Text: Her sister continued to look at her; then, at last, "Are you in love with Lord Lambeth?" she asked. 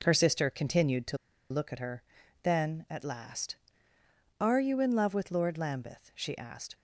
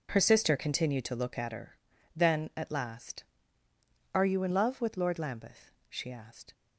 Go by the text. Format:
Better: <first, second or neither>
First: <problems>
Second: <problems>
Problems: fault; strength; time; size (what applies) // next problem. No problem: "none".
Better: second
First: pauses between "to" and "look"; slight; at 1.1 s; 0.34 s long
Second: none